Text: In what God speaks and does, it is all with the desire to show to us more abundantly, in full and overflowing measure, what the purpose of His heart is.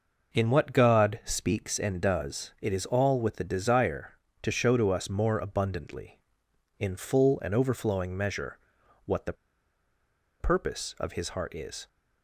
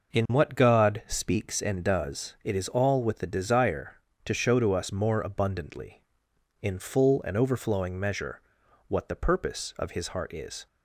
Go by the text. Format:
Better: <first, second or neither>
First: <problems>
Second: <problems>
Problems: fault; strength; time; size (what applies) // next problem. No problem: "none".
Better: second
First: pauses between "the" and "purpose"; at 9.3 s; 1.0 s long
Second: none